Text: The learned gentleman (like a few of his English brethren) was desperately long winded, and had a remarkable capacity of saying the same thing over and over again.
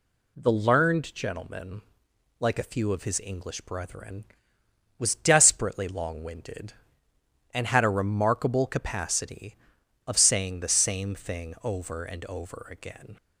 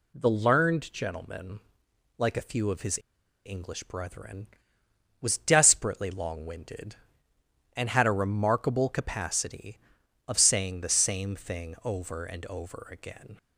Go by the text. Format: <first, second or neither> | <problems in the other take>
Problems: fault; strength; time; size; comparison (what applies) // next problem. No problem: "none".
first | pauses between "his" and "English"; noticeable; at 2.9 s; 0.46 s long